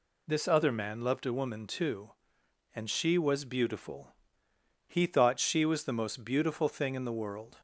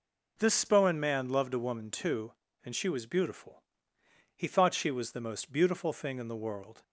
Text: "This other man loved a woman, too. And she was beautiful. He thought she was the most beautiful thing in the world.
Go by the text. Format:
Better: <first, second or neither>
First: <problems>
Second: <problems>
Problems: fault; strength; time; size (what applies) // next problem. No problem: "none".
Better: first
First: none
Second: says "spohen" for "other"; at 0.5 s